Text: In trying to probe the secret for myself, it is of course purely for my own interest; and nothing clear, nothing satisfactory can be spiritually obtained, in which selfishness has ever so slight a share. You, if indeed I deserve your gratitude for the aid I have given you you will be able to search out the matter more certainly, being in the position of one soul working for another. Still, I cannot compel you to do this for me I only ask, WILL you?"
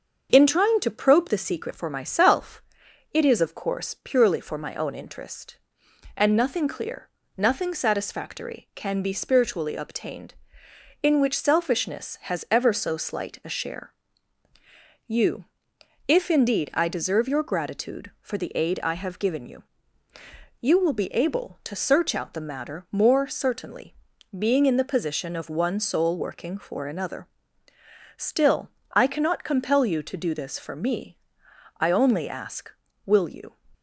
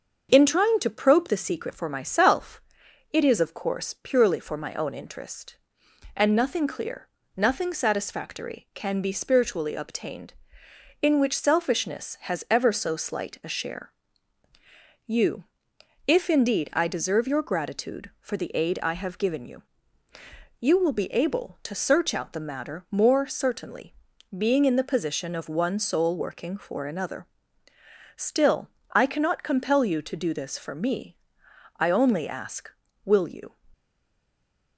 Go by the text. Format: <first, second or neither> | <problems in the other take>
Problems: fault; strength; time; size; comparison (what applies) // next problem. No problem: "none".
first | starts louder than the rest; until 1.3 s; 6.5 dB; also in the first // pauses between "you" and "you"; at 19.6 s; 1.0 s long; also in the first // pauses between "me" and "I"; noticeable; at 31.1 s; 0.62 s long; noticeable in the first // stays silent after the last word; from 33.7 s on; 1.0 s long